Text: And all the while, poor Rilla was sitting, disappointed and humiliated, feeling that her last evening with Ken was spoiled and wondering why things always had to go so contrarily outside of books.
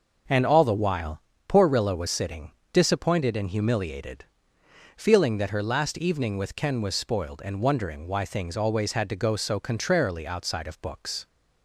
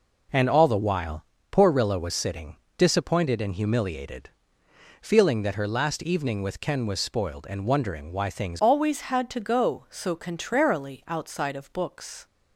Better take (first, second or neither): first